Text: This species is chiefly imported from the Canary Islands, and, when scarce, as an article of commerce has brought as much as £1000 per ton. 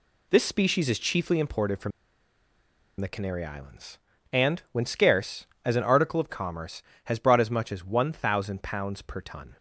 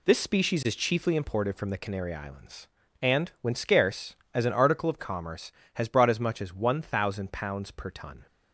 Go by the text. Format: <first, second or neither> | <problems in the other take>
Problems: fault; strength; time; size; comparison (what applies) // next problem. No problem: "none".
second | pauses between "from" and "the"; at 1.9 s; 1.0 s long